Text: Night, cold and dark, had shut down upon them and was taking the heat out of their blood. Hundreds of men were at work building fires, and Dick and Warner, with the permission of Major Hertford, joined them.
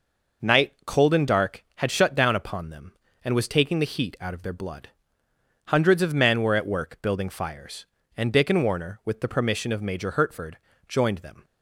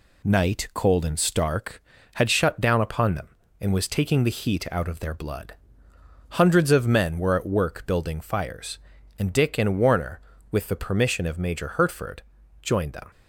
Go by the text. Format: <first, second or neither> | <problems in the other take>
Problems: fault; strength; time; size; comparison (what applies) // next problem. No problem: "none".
first | says "stark" for "dark"; at 1.1 s